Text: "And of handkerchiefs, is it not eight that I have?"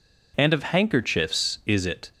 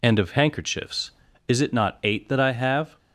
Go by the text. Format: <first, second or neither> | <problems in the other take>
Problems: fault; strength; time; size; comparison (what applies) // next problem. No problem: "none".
second | stops before "not eight that I have"; at 2.1 s